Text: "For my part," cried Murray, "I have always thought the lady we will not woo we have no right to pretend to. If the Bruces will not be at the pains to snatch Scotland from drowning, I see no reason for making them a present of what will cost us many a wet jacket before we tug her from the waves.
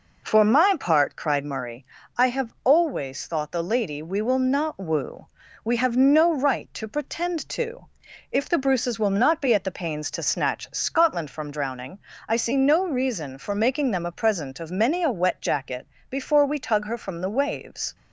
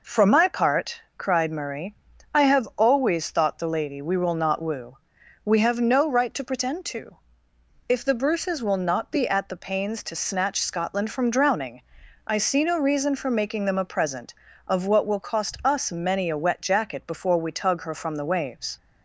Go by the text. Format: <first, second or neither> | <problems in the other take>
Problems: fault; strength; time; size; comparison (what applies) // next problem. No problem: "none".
second | pauses between "woo" and "we"; at 5.2 s; 0.38 s long; noticeable in the second // skips "what will cost us"; at 14.7 s // pauses between "jacket" and "before"; slight; at 15.8 s; 0.20 s long